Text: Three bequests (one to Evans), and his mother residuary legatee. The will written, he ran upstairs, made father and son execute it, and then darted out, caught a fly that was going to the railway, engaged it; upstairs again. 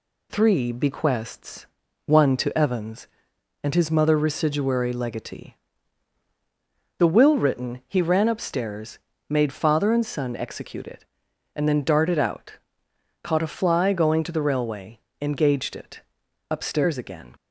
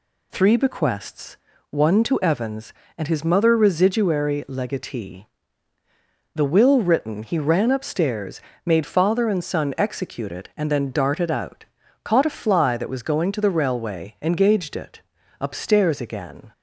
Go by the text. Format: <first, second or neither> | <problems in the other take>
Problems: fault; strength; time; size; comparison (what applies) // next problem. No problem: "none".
second | skips "that was"; at 13.9 s